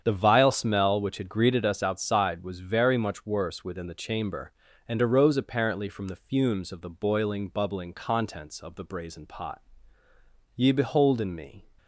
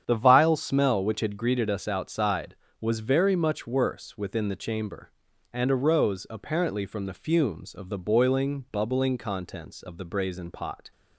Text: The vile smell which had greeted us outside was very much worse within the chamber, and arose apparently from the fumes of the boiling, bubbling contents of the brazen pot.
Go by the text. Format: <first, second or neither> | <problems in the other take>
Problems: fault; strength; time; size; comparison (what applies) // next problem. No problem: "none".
second | starts louder than the rest; strong; until 1.0 s; 8 dB; strong in the second // goes on to say "Ye behold in me"; noticeable; from 10.5 s on; 1.1 s long